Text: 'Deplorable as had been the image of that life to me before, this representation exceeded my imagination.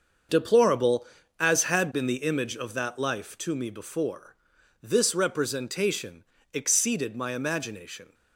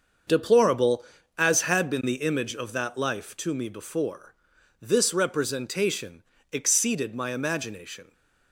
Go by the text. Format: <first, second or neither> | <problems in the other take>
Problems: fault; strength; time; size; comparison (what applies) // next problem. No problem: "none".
neither | starts louder than the rest; the same in both // pauses between "representation" and "exceeded"; slight; the same in both